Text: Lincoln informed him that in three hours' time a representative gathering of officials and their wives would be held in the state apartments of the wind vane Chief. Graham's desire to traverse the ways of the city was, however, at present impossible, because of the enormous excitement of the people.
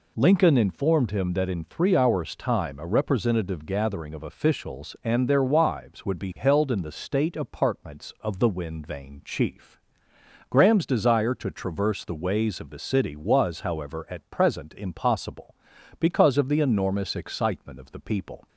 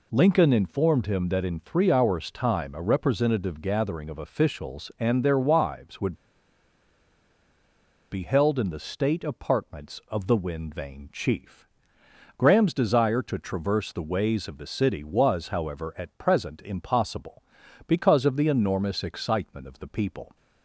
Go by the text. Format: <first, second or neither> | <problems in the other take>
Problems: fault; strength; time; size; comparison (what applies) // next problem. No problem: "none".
first | pauses between "would" and "be"; strong; at 6.1 s; 1.9 s long